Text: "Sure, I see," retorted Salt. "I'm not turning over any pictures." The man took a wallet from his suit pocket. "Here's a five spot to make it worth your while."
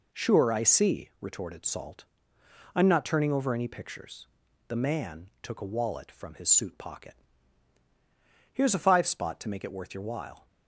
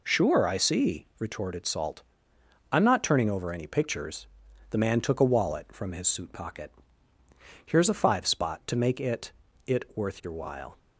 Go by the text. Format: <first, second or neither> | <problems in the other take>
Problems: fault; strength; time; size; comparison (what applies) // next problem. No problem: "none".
first | says "it" twice; at 9.6 s